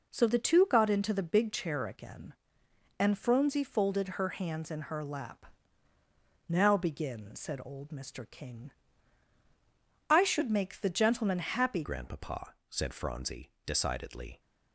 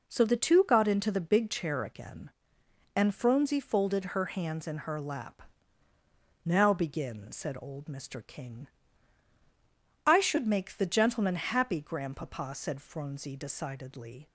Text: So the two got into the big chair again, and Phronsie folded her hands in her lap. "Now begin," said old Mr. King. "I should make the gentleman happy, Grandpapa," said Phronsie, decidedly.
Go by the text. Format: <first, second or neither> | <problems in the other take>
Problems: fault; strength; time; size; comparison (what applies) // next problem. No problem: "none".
second | changes voice at "Grandpapa"; from 11.8 s on; 2.5 s long